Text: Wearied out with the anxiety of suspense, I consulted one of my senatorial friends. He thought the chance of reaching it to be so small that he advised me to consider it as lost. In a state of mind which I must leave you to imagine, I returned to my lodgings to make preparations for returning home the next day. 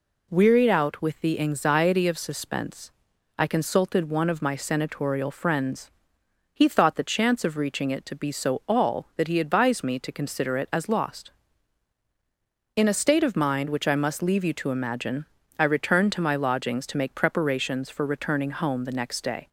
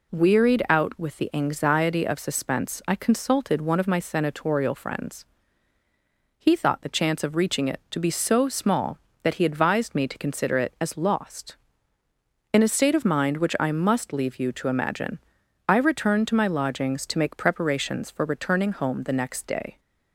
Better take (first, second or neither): second